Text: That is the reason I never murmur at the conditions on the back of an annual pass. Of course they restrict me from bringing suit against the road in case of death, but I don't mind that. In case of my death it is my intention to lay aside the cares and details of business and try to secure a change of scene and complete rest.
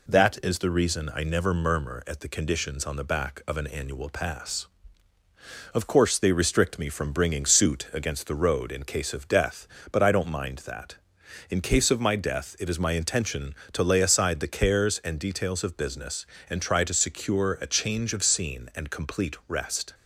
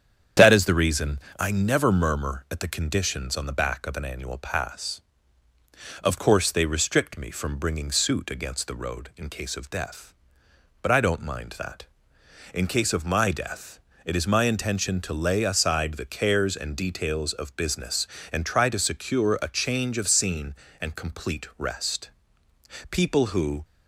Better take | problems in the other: first | starts louder than the rest; strong; until 1.5 s; 8.5 dB // pauses between "reason" and "I"; slight; at 1.1 s; 0.22 s long // pauses between "death" and "it"; slight; at 13.8 s; 0.24 s long // goes on to say "People who"; noticeable; from 22.9 s on; 0.72 s long

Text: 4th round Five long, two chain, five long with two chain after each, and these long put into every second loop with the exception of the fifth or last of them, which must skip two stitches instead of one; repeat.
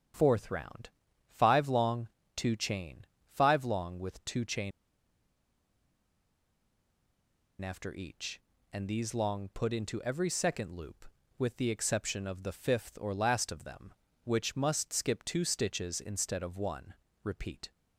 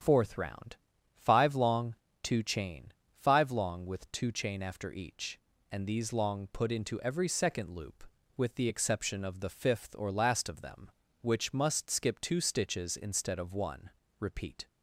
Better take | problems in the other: second | starts louder than the rest; strong; until 1.5 s; 8 dB; strong in the second // pauses between "round" and "Five"; slight; at 0.9 s; 0.36 s long; slight in the second // pauses between "chain" and "after"; strong; at 4.7 s; 2.9 s long

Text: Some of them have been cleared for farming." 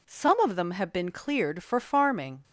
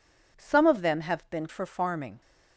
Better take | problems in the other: first | skips "cleared"; at 1.4 s

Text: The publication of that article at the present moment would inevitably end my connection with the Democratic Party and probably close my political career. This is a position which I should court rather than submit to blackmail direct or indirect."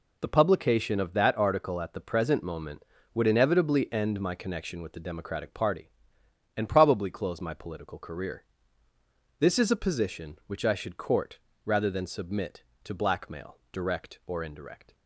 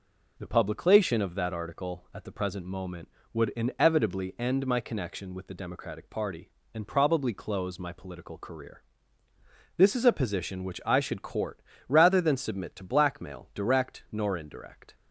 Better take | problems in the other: first | pauses between "court" and "rather"; slight; at 11.6 s; 0.26 s long; slight in the first // says "nor" for "or"; at 14.1 s

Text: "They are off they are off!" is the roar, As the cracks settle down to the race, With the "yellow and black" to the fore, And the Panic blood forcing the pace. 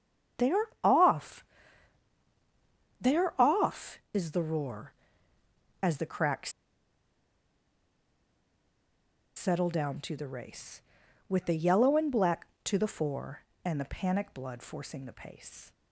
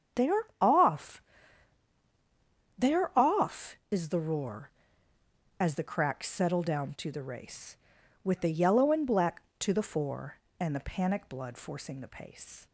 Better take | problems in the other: second | starts louder than the rest; strong; until 3.0 s; 7.5 dB; strong in the second // pauses between "off" and "they"; strong; at 1.4 s; 1.5 s long; strong in the second // pauses between "cracks" and "settle"; strong; at 6.5 s; 2.8 s long

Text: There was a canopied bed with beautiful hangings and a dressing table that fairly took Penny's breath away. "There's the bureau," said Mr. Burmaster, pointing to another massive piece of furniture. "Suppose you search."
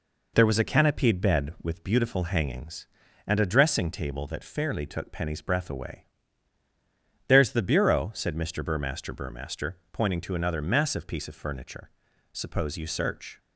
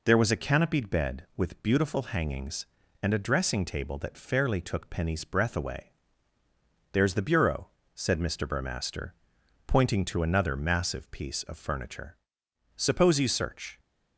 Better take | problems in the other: second | says "Burmaster" twice; at 9.1 s

